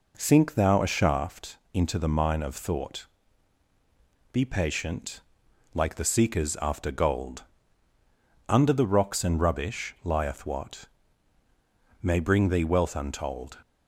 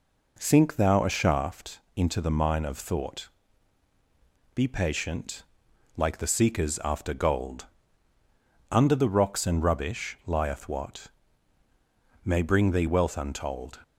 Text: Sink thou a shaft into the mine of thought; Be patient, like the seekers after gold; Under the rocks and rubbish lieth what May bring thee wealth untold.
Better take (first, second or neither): neither